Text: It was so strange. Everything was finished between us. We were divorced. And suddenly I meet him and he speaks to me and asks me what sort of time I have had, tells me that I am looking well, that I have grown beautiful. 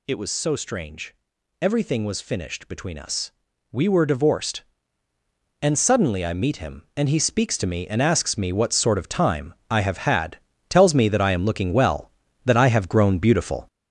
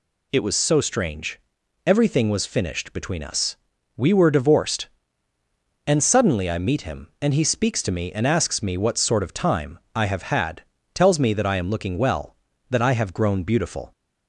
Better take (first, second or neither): second